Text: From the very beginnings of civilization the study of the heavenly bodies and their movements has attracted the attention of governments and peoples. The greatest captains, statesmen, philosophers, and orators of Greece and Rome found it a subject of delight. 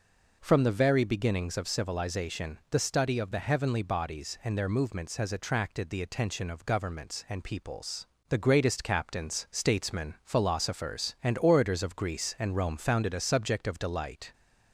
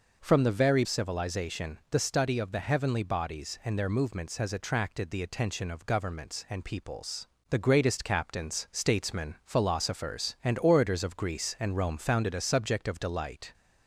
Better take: first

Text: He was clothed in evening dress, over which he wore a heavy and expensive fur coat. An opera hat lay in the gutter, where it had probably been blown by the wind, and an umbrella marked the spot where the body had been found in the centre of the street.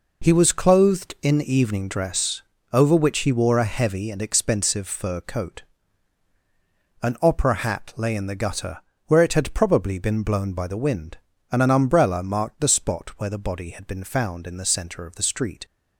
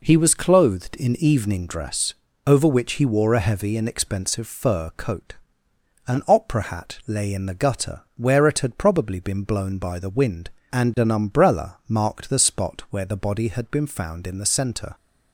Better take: first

